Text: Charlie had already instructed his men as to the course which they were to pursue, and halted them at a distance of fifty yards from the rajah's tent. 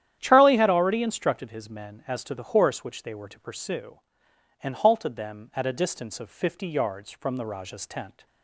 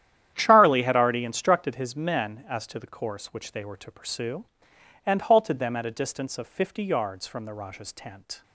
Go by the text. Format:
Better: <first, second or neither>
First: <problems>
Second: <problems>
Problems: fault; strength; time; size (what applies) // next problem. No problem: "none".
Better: second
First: starts louder than the rest; strong; until 1.2 s; 10.5 dB // says "horse" for "course"; at 2.5 s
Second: starts louder than the rest; strong; until 1.3 s; 10.5 dB